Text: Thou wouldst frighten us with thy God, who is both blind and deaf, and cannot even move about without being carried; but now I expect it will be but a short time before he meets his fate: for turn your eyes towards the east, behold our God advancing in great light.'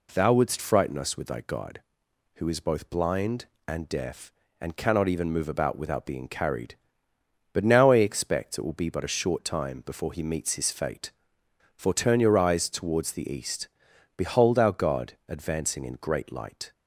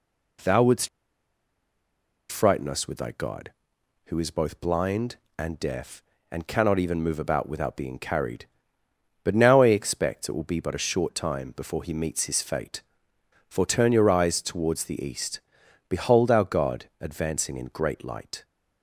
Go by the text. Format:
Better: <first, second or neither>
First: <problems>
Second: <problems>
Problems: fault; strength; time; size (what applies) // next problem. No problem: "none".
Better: first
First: pauses between "God" and "advancing"; slight; at 15.1 s; 0.16 s long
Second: pauses between "wouldst" and "frighten"; strong; at 0.8 s; 1.4 s long // pauses between "God" and "advancing"; slight; at 16.8 s; 0.16 s long